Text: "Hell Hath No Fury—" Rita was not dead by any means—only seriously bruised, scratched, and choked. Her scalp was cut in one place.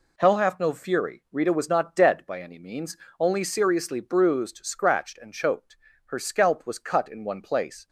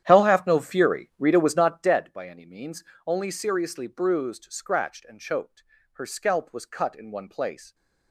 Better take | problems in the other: first | starts louder than the rest; strong; until 1.9 s; 10.5 dB

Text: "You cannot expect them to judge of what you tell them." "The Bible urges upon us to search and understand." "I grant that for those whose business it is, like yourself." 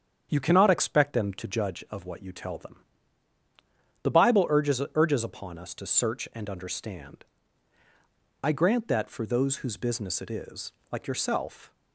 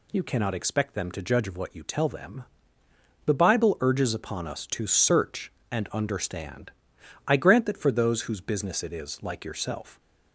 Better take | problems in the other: second | starts louder than the rest; strong; until 1.3 s; 8 dB // says "urges" twice; at 4.9 s

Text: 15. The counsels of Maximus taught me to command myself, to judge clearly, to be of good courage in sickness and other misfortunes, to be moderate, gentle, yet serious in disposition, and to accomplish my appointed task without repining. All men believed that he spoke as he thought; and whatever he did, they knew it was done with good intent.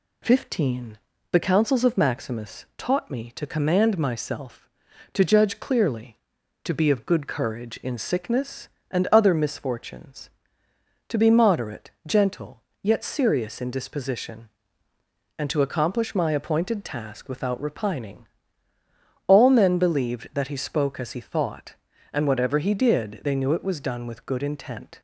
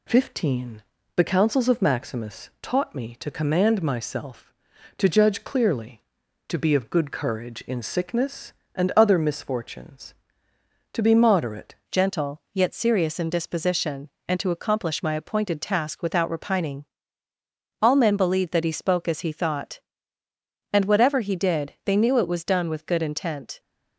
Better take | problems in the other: first | changes voice at "gentle"; from 11.9 s on; 11.6 s long

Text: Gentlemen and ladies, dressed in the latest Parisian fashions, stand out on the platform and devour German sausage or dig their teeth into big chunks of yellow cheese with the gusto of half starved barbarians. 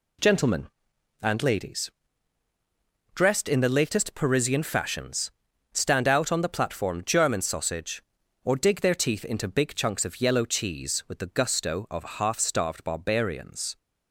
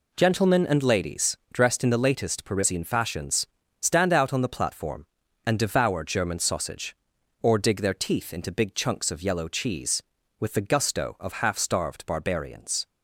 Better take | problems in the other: second | skips "and devour"; at 7.0 s

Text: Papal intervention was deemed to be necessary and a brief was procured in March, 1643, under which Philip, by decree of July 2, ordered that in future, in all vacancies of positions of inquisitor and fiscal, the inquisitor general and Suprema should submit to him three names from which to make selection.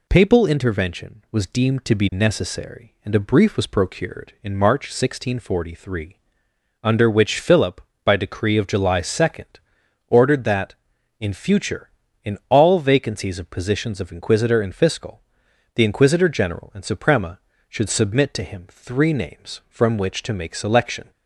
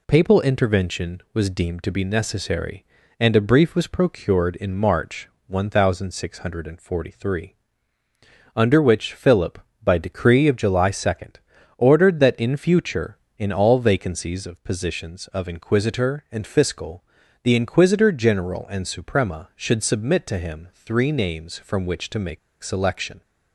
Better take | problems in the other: first | pauses between "make" and "selection"; slight; at 22.3 s; 0.23 s long

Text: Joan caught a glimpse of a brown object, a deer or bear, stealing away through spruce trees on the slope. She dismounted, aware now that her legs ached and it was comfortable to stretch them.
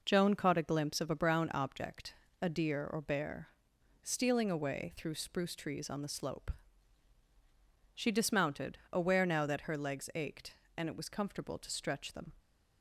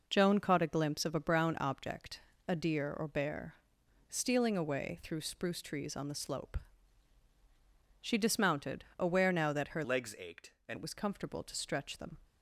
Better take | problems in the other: first | changes voice from "legs" to "and"; from 9.8 to 10.7 s; 0.9 s long

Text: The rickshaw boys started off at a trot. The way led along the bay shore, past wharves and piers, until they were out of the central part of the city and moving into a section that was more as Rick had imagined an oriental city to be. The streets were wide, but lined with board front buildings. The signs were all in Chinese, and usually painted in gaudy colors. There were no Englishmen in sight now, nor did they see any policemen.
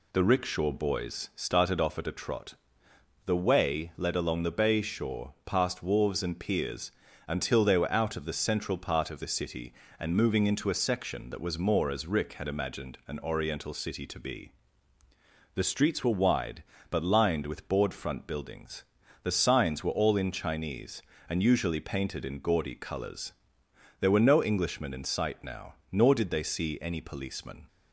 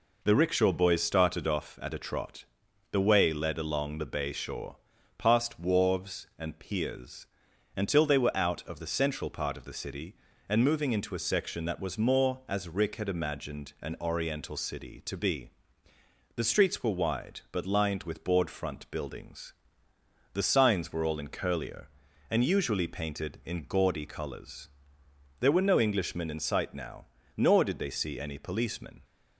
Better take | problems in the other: first | says "Curlier" for "Chinese"; at 21.2 s

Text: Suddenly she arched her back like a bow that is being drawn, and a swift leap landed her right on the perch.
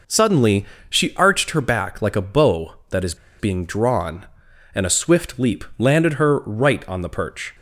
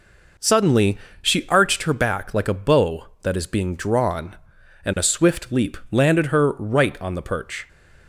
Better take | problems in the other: second | pauses between "Suddenly" and "she"; slight; at 0.6 s; 0.24 s long; slight in the second // pauses between "is" and "being"; slight; at 3.1 s; 0.24 s long // pauses between "leap" and "landed"; slight; at 5.6 s; 0.16 s long; slight in the second

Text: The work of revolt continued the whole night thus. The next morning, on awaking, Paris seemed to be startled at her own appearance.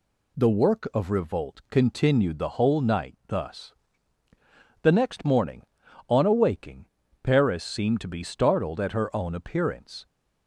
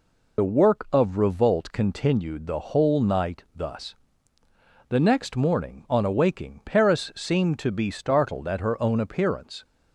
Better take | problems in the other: first | loses the start of "The"; at 0.3 s; 50 ms

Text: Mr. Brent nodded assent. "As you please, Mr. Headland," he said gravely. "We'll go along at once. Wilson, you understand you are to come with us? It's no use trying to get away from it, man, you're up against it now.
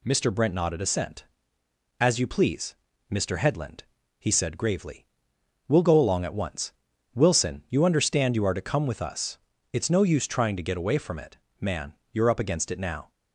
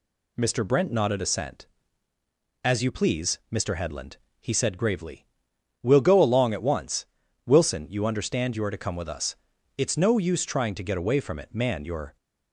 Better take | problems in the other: first | stops before "up against it now"; at 12.1 s

